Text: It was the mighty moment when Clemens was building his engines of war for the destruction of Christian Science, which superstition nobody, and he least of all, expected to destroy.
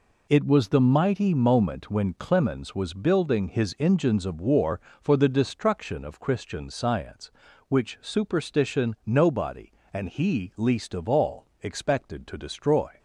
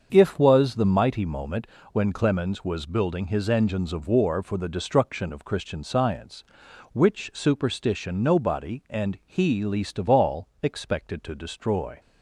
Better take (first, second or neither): first